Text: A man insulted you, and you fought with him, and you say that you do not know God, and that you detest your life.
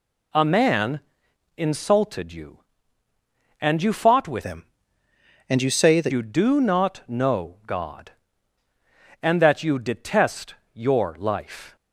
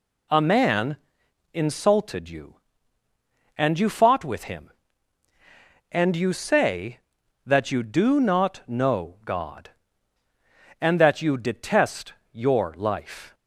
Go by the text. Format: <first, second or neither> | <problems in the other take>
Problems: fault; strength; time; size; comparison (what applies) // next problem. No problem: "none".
second | pauses between "man" and "insulted"; noticeable; at 0.9 s; 0.56 s long; noticeable in the second // changes voice from "him" to "that"; from 4.4 to 6.1 s; 1.7 s long // pauses between "detest" and "your"; slight; at 10.5 s; 0.18 s long; slight in the second